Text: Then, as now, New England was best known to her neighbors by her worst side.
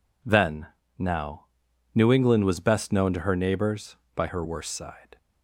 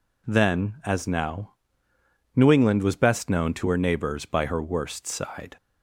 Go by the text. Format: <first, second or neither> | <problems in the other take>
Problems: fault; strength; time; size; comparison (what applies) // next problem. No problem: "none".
second | skips "as"; at 0.8 s